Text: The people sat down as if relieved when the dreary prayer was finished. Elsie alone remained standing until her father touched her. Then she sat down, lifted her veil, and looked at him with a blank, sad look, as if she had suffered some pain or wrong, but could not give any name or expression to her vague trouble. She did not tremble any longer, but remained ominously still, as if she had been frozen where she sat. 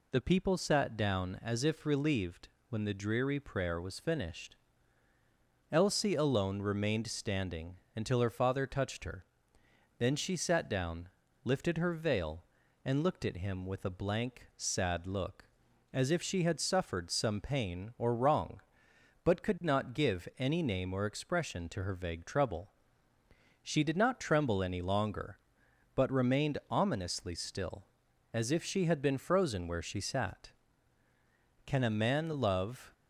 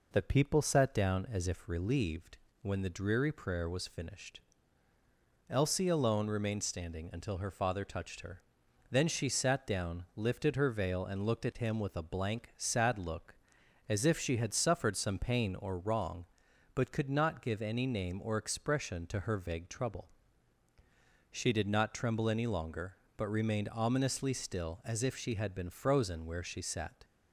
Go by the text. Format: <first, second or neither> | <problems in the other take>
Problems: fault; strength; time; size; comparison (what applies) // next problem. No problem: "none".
second | pauses between "relieved" and "when"; slight; at 2.4 s; 0.22 s long; slight in the second // pauses between "standing" and "until"; slight; at 7.7 s; 0.18 s long // goes on to say "Can a man love"; noticeable; from 31.6 s on; 1.2 s long